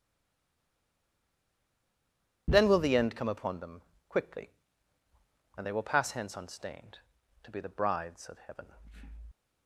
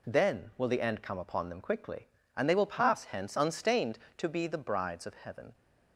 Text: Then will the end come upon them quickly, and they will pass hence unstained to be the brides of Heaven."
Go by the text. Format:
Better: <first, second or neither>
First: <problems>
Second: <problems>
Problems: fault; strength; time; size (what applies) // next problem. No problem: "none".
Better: second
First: stays silent before the first word; until 2.4 s; 2.4 s long // pauses between "them" and "quickly"; slight; at 3.8 s; 0.24 s long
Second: none